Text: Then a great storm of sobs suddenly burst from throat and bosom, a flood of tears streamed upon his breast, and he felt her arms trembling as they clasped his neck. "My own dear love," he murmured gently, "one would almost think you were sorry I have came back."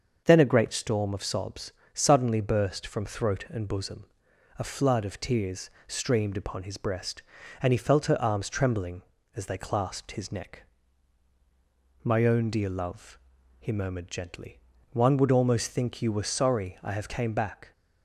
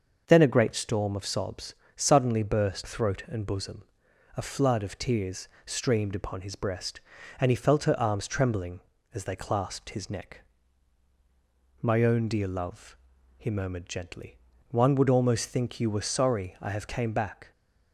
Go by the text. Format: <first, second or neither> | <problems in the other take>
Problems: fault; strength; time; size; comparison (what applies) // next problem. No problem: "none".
first | starts louder than the rest; until 1.2 s; 6.5 dB; also in the first // pauses between "sobs" and "suddenly"; slight; at 1.7 s; 0.22 s long; slight in the first // skips "from"; at 2.8 s // pauses between "tears" and "streamed"; slight; at 5.4 s; 0.16 s long; slight in the first